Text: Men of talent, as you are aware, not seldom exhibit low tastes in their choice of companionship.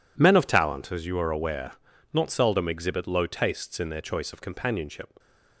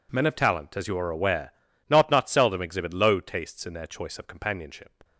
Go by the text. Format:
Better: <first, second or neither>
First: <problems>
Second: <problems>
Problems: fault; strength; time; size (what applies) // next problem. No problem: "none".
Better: first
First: none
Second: says "not" twice; at 2.1 s